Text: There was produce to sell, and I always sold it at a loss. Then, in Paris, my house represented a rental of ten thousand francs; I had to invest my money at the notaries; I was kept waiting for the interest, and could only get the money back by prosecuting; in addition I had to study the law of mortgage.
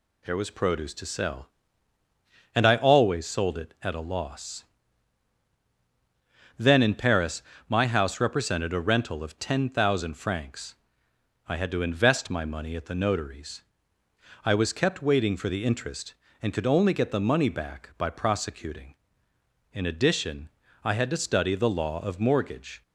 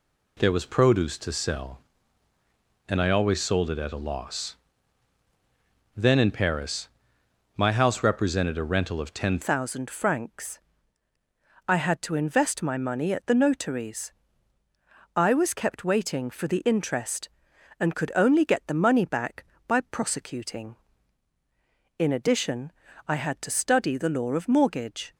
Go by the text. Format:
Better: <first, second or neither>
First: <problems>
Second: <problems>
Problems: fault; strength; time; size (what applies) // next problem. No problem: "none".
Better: first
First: pauses between "addition" and "I"; slight; at 20.4 s; 0.34 s long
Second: changes voice at "thousand"; from 9.4 s on; 15.7 s long // pauses between "addition" and "I"; slight; at 22.7 s; 0.34 s long